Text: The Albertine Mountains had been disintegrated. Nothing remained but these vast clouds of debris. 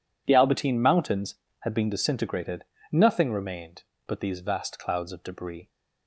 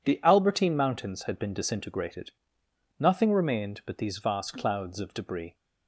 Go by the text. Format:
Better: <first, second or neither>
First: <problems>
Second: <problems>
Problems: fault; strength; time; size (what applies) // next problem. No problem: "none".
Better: neither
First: none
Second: none